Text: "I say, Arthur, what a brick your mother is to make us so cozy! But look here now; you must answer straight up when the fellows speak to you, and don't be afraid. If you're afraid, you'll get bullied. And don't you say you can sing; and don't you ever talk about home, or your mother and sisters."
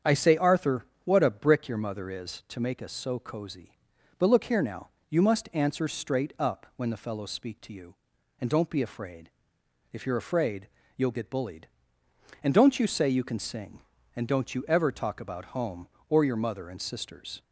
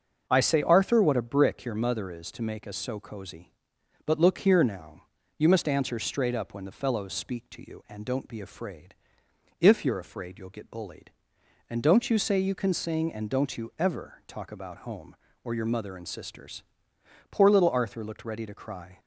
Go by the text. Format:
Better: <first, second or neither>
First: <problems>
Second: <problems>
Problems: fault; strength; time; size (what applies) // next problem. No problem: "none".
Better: first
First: starts louder than the rest; strong; until 1.2 s; 7.5 dB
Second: starts louder than the rest; until 1.2 s; 6 dB // goes on to say "Poor little Arthur looked ready to cry"; strong; from 17.3 s on; 1.6 s long